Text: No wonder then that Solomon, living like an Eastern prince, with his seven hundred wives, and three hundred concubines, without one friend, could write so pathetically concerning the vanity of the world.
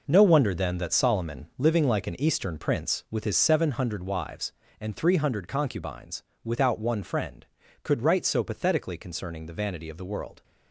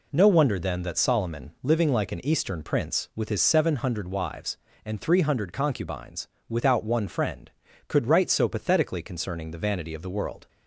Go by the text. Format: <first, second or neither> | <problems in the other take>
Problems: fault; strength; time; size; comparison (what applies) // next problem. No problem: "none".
second | gets quieter; strong; throughout; 10 dB